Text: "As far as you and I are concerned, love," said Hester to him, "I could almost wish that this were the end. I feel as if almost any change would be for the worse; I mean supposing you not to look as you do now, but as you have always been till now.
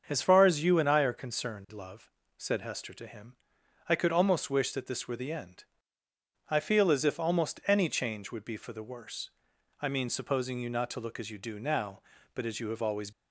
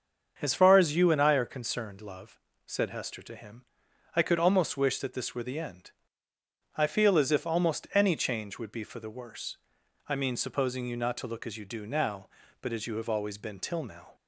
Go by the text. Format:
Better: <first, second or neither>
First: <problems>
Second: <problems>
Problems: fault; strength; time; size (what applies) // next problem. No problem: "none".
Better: second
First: starts louder than the rest; until 1.0 s; 7 dB // stops before "been till now"; at 13.1 s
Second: starts louder than the rest; until 1.3 s; 7 dB